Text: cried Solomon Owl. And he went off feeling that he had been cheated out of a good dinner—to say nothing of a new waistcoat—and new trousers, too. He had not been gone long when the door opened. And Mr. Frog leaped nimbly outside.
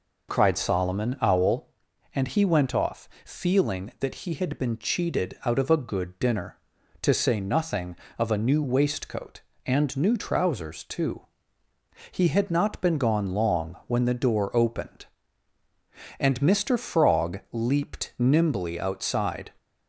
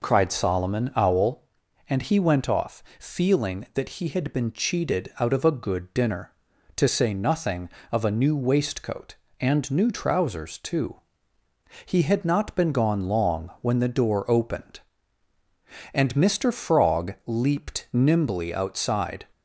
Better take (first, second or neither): neither